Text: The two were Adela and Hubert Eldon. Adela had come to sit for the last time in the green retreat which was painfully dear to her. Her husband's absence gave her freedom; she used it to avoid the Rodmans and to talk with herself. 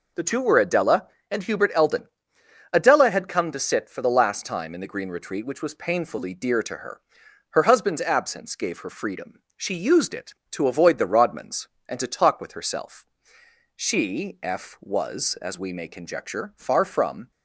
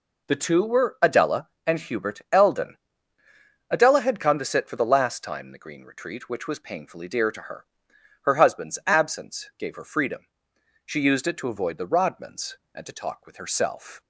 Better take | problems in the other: second | goes on to say "She F was as we may conjecture far from"; strong; from 13.7 s on; 3.5 s long

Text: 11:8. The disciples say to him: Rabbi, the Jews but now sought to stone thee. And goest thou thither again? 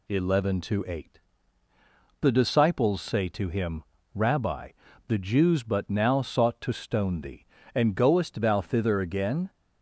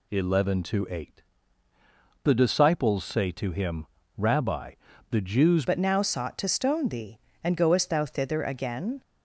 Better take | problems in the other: first | changes voice at "but"; from 5.6 s on; 3.4 s long

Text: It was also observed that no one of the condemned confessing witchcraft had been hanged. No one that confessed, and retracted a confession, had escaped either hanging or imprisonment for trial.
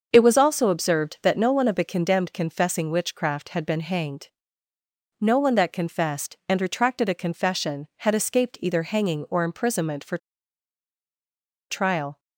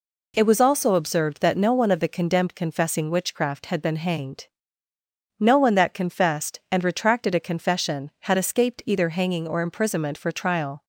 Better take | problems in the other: second | starts louder than the rest; until 1.1 s; 6.5 dB // pauses between "for" and "trial"; strong; at 10.1 s; 1.5 s long

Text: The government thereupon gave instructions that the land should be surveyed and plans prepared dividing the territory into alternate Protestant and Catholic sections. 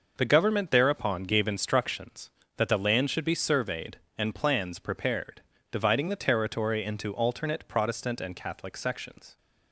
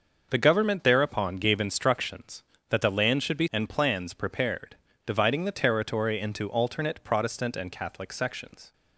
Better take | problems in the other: first | starts louder than the rest; noticeable; until 1.3 s; 6 dB // skips "surveyed"; at 3.4 s // pauses between "prepared" and "dividing"; slight; at 4.7 s; 0.30 s long; slight in the first

